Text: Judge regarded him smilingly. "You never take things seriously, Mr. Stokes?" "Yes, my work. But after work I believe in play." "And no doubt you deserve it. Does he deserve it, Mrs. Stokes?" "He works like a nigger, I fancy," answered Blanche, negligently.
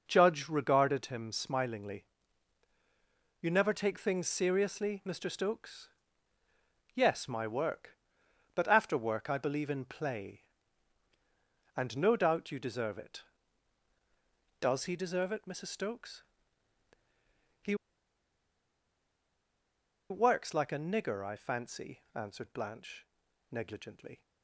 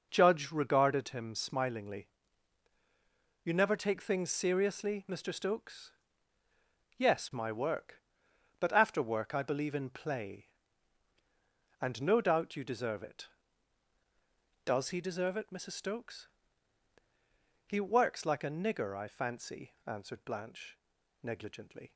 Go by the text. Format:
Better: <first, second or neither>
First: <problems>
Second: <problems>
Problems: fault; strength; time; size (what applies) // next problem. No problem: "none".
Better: second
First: pauses between "He" and "works"; strong; at 17.7 s; 2.3 s long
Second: none